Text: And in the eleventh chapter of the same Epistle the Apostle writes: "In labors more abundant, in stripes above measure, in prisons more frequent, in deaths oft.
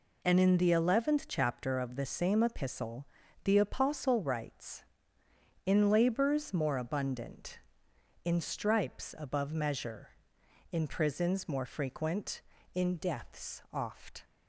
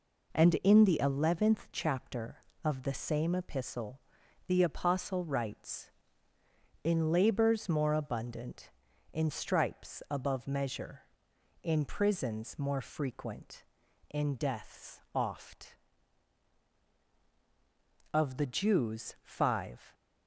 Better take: first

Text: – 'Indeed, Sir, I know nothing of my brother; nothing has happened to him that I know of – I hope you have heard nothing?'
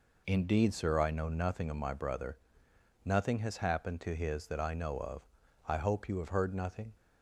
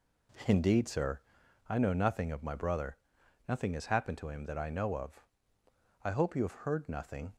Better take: second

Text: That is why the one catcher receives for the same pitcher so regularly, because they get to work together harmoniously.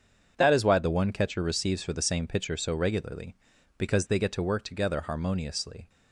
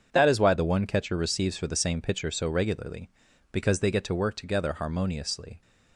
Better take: neither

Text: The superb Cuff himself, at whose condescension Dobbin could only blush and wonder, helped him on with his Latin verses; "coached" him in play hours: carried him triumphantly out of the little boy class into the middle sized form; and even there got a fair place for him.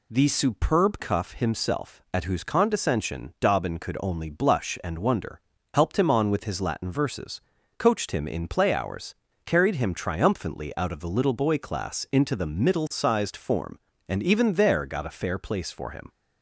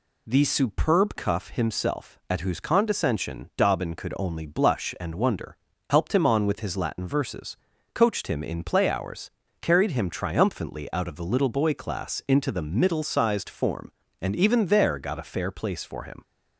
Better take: neither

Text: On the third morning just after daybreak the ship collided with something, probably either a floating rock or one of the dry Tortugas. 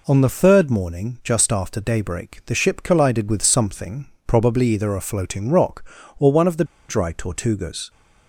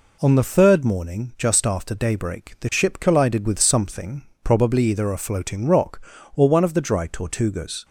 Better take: second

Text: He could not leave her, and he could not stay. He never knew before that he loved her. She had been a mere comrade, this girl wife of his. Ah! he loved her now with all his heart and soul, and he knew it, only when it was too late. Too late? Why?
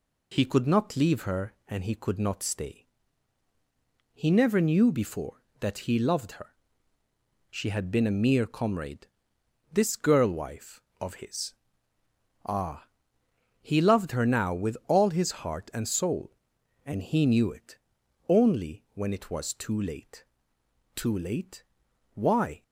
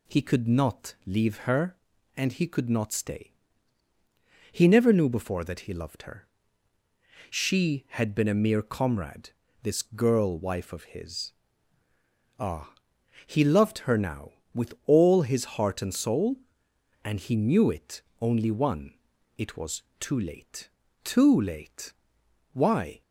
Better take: first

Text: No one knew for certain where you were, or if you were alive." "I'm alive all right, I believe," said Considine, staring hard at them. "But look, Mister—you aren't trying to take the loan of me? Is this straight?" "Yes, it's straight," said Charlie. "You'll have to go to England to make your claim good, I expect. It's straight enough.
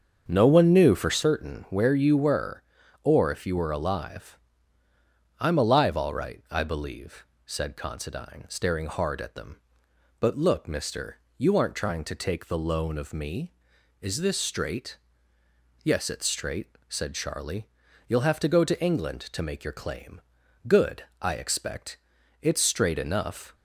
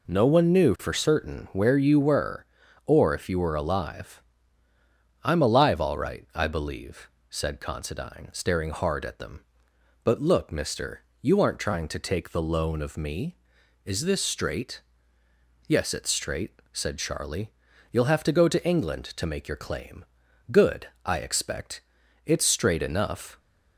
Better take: second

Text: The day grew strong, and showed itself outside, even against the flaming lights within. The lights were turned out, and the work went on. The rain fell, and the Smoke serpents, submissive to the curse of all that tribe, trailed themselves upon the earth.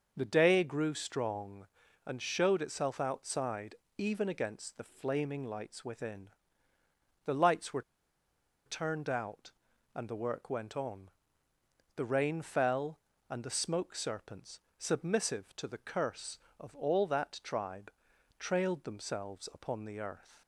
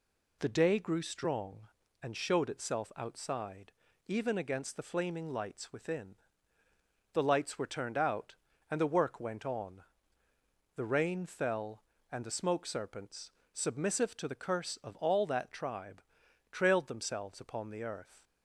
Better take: second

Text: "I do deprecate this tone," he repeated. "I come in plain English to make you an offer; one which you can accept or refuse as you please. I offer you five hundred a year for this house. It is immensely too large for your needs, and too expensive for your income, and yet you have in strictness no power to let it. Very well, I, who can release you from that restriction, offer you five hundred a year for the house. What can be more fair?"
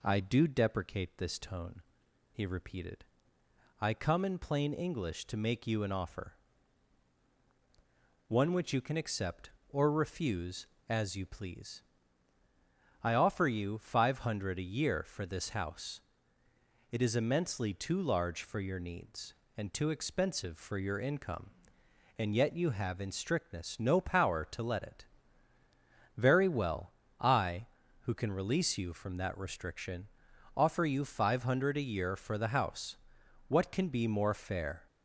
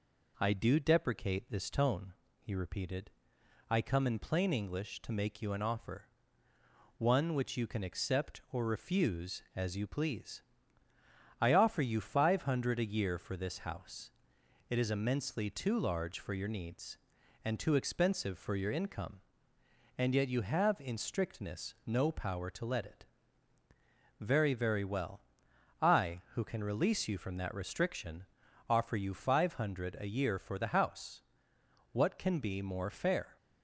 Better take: first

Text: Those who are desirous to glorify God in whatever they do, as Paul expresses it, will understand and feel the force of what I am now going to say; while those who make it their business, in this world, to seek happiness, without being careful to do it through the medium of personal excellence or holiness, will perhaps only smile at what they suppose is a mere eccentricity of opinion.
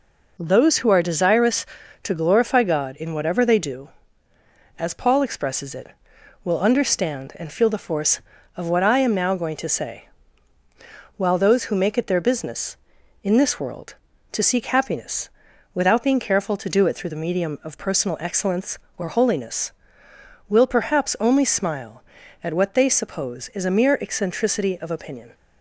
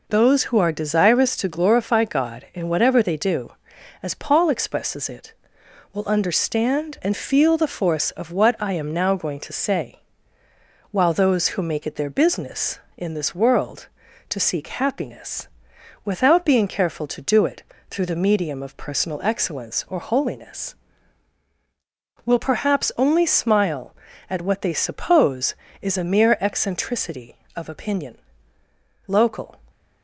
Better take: first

